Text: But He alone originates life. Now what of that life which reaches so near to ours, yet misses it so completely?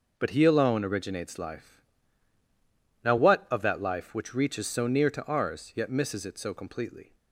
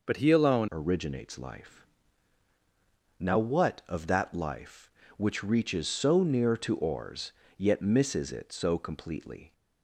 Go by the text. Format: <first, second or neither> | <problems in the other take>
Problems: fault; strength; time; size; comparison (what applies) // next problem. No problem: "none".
first | changes voice at "originates"; from 0.7 s on; 8.8 s long